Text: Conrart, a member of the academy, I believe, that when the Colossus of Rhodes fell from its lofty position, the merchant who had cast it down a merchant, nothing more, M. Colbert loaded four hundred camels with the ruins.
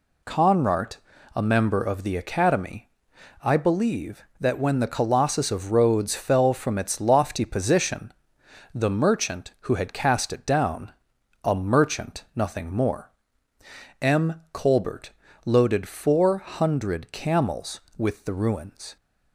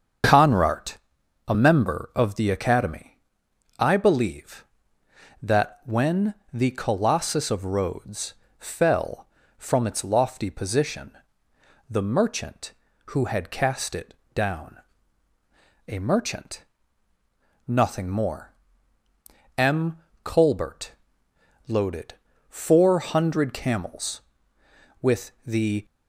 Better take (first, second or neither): first